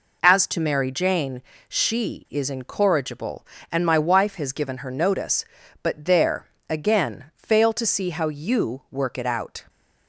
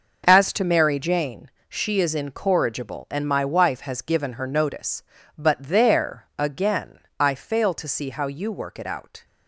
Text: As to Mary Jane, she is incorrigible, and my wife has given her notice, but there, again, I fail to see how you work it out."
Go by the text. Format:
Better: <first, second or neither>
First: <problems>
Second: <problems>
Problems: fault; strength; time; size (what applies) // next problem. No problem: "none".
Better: second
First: skips "I"; at 7.3 s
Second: none